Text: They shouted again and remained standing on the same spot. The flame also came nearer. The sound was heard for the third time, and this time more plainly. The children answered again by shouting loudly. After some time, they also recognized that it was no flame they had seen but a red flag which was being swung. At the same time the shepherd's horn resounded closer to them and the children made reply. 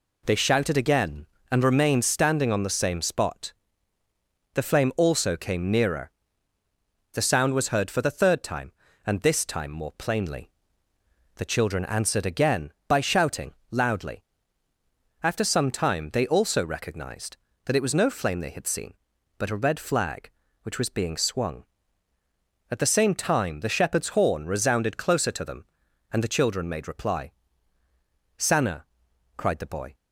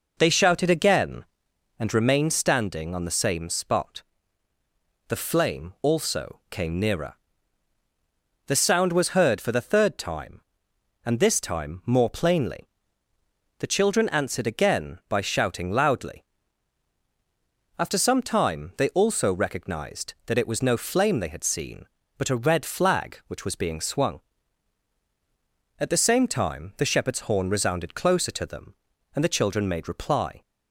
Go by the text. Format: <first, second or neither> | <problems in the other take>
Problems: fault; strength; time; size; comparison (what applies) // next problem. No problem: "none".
second | pauses between "shouting" and "loudly"; slight; at 13.5 s; 0.18 s long // goes on to say "Sanna cried the boy"; from 28.3 s on; 1.5 s long